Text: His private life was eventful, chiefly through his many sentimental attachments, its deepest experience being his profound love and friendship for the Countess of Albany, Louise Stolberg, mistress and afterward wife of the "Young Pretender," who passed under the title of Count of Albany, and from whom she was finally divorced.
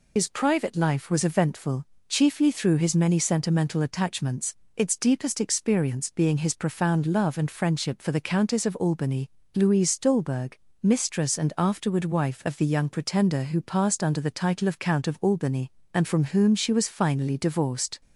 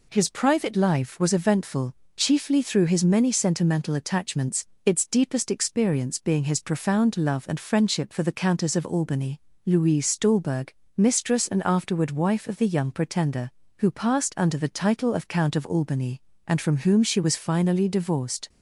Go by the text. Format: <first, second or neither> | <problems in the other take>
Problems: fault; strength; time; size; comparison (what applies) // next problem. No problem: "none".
second | loses the start of "His"; at 0.1 s; 55 ms